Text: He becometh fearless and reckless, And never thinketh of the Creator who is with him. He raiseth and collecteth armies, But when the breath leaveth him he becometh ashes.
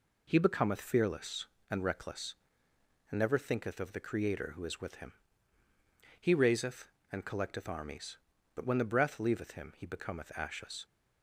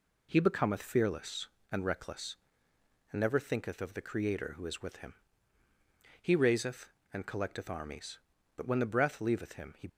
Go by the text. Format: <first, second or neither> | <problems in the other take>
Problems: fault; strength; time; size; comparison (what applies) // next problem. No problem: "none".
first | stops before "becometh ashes"; at 9.8 s